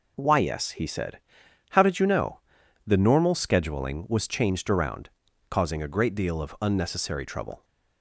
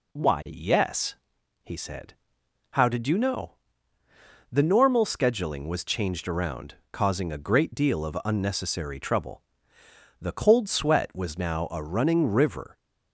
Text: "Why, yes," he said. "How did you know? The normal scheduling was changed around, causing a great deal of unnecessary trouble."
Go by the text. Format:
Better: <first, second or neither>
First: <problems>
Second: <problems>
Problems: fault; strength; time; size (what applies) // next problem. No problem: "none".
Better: first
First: none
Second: goes on to say "The cold sweat was now a running river"; strong; from 10.1 s on; 2.5 s long